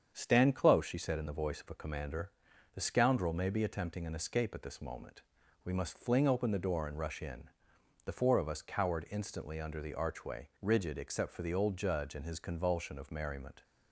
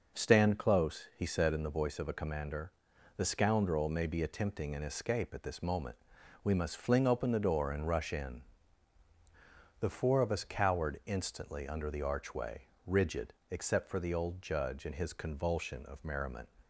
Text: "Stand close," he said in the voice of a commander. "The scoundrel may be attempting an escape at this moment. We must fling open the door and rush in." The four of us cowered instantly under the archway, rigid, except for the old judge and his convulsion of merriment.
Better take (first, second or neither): second